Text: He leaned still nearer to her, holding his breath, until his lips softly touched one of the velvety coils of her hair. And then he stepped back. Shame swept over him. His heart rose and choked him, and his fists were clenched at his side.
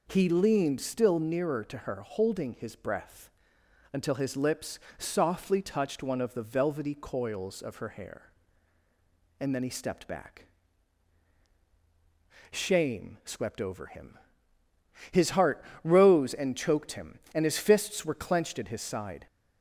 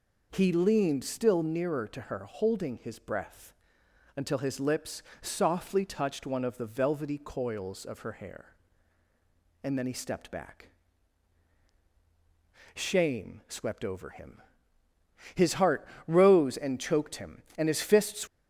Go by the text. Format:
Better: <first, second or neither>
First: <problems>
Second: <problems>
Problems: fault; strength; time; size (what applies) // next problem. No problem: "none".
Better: first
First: pauses between "lips" and "softly"; slight; at 4.7 s; 0.20 s long // pauses between "heart" and "rose"; slight; at 15.6 s; 0.20 s long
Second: pauses between "lips" and "softly"; slight; at 5.0 s; 0.20 s long // pauses between "heart" and "rose"; slight; at 15.8 s; 0.20 s long // stops before "were clenched at his side"; at 18.2 s